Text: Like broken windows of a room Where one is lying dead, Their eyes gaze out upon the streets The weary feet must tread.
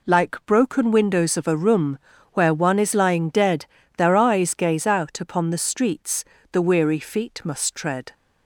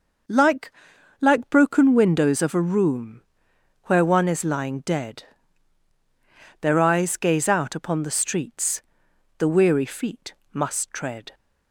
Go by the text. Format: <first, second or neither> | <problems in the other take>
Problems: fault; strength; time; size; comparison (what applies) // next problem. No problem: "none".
first | says "Like" twice; at 1.1 s // pauses between "room" and "Where"; noticeable; at 3.1 s; 0.68 s long; slight in the first // pauses between "streets" and "The"; noticeable; at 8.7 s; 0.58 s long; slight in the first // pauses between "feet" and "must"; slight; at 10.3 s; 0.22 s long